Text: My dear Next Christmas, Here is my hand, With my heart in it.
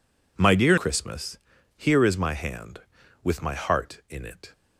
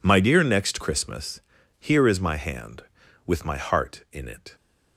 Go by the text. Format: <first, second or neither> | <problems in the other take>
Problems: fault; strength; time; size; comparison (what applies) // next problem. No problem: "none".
second | skips "Next"; at 0.7 s